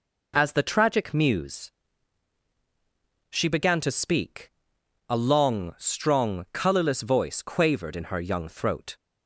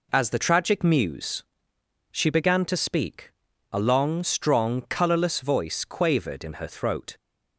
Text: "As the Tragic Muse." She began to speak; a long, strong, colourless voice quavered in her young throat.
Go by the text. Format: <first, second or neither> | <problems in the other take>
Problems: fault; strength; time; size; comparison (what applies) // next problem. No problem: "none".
first | skips "young"; at 6.6 s